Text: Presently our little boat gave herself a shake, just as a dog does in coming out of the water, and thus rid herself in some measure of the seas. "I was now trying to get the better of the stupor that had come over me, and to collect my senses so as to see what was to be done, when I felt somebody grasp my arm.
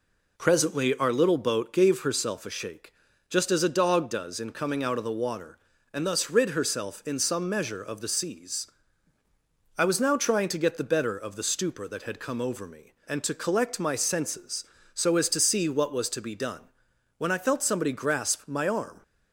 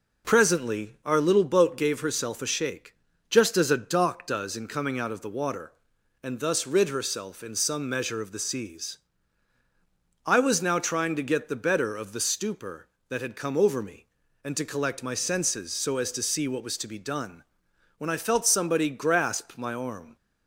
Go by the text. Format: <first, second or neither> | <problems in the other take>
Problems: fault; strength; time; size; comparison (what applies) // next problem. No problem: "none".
first | says "dock" for "dog"; at 3.7 s